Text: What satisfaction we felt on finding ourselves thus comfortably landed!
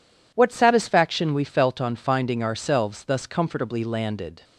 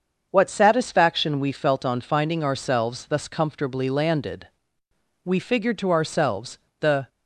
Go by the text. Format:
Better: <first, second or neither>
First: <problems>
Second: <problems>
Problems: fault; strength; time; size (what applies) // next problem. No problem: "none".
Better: first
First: none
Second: starts louder than the rest; until 1.3 s; 7 dB // goes on to say "We figured to ourselves the"; strong; from 5.2 s on; 1.8 s long